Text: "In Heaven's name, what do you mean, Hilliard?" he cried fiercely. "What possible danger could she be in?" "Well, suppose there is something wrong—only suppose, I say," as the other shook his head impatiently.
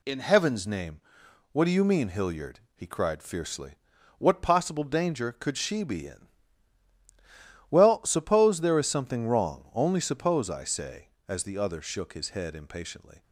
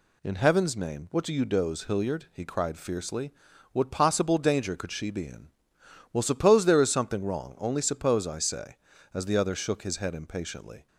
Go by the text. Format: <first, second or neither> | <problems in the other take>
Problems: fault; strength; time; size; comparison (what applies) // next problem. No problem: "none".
first | says "doze" for "mean"; at 1.4 s